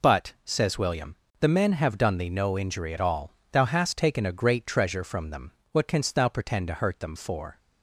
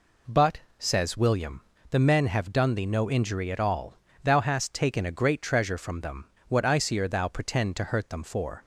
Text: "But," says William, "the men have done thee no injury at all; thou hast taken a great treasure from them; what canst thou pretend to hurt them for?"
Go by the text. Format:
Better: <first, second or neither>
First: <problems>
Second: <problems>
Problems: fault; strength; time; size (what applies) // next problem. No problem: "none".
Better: first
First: none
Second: says "icier" for "canst"; at 6.6 s